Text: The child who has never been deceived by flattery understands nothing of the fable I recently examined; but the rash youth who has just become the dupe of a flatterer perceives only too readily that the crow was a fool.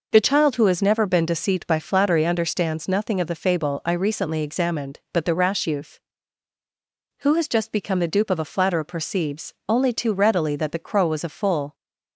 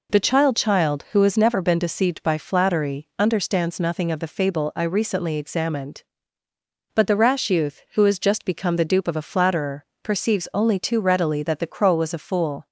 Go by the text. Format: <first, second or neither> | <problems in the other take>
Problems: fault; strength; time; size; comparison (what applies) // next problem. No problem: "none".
first | says "child" twice; at 0.5 s // pauses between "flatterer" and "perceives"; slight; at 9.8 s; 0.18 s long